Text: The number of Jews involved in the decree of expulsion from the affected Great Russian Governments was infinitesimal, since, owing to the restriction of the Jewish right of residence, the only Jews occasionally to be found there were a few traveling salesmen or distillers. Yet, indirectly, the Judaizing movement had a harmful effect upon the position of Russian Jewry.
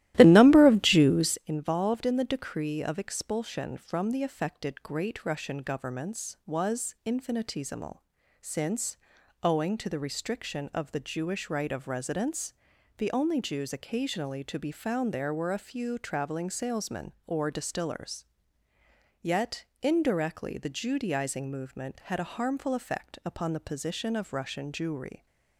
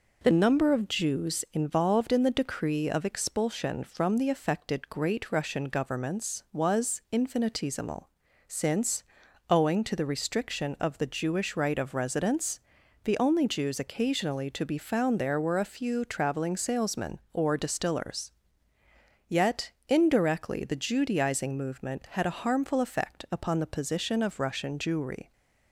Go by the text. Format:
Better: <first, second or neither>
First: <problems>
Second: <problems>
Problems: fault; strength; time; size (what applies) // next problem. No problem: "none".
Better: second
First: starts louder than the rest; strong; until 1.5 s; 15.5 dB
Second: none